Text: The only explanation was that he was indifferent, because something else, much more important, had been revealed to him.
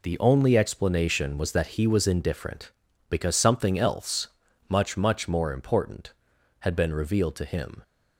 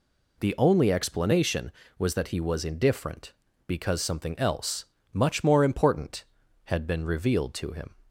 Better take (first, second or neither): second